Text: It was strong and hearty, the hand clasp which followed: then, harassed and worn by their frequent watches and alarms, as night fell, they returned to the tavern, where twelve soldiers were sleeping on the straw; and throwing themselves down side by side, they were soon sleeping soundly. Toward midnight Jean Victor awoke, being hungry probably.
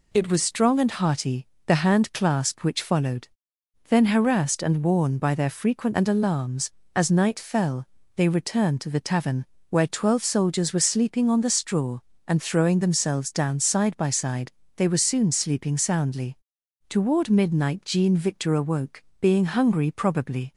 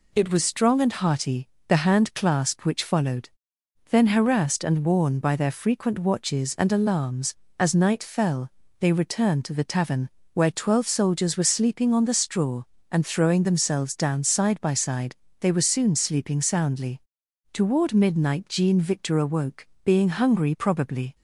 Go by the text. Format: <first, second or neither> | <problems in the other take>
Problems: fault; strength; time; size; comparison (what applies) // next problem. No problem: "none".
second | skips "watches"; at 5.9 s